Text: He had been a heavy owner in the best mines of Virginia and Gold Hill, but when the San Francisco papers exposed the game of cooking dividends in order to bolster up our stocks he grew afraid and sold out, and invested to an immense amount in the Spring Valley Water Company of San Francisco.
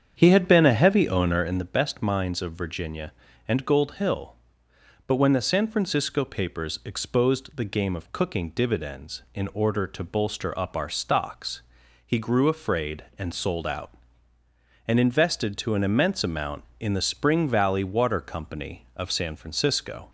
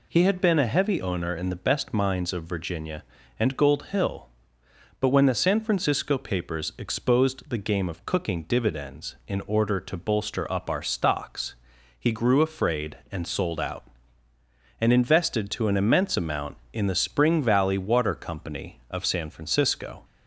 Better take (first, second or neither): second